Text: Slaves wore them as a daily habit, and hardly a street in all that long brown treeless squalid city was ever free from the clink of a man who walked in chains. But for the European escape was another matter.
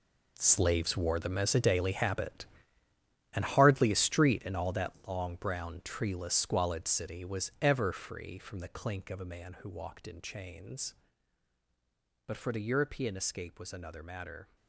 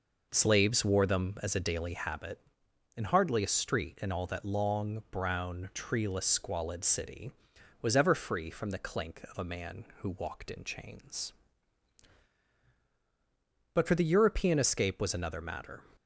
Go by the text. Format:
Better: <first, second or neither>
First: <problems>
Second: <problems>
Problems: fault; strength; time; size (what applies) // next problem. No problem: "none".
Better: second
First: gets quieter; strong; throughout; 13.5 dB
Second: none